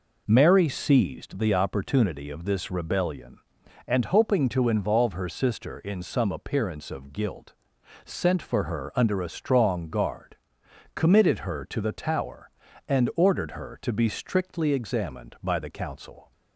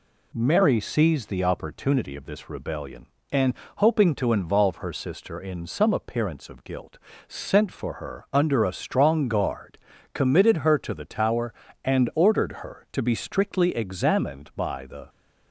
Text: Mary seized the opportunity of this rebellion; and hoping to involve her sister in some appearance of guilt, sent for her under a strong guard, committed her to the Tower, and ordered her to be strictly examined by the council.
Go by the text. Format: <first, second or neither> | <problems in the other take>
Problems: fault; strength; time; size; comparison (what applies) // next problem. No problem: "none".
first | pauses between "and" and "hoping"; slight; at 3.5 s; 0.22 s long // stops before "council"; at 15.0 s